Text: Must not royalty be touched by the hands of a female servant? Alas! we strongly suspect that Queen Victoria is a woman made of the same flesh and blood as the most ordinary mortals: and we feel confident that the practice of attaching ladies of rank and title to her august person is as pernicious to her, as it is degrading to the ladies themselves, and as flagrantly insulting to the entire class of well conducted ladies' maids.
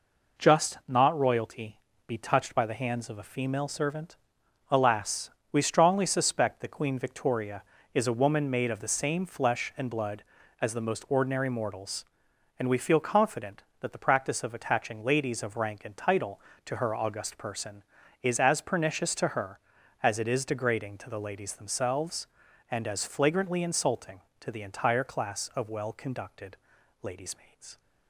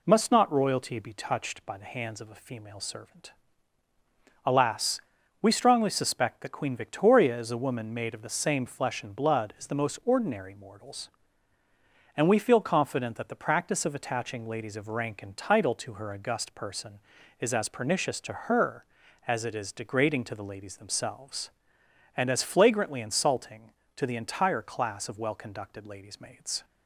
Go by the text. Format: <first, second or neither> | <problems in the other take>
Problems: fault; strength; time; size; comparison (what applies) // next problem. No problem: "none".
second | says "Just" for "Must"; at 0.3 s // pauses between "royalty" and "be"; slight; at 1.7 s; 0.26 s long // pauses between "conducted" and "ladies"; at 26.5 s; 0.44 s long